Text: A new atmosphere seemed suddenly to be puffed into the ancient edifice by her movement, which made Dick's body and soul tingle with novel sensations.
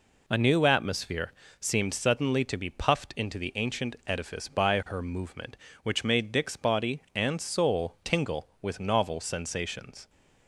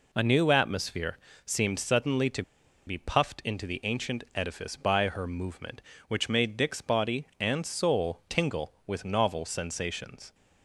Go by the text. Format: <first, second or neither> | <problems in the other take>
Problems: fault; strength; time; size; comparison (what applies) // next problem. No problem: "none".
first | pauses between "atmosphere" and "seemed"; slight; at 1.1 s; 0.28 s long; slight in the first // pauses between "to" and "be"; at 2.4 s; 0.45 s long